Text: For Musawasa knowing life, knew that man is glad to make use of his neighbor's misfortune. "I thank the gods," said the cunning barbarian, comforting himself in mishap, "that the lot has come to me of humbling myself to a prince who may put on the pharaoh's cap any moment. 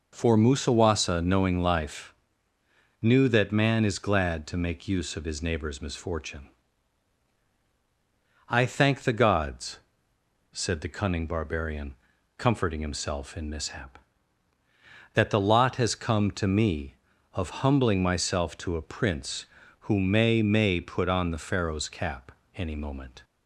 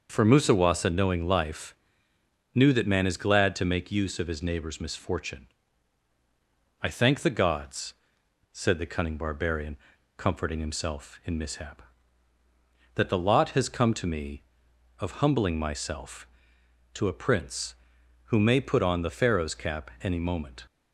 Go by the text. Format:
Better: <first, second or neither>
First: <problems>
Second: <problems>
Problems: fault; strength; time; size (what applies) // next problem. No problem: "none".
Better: second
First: says "may" twice; at 20.4 s // pauses between "cap" and "any"; slight; at 22.2 s; 0.24 s long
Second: none